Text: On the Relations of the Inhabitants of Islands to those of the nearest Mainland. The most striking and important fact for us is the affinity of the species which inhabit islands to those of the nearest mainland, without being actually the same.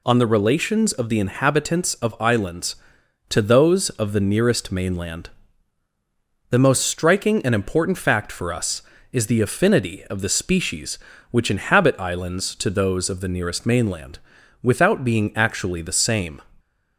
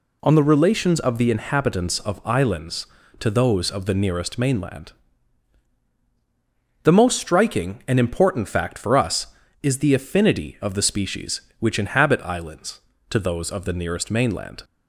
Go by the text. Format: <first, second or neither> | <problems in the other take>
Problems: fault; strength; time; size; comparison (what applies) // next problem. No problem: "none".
first | stops before "without being actually the same"; at 14.6 s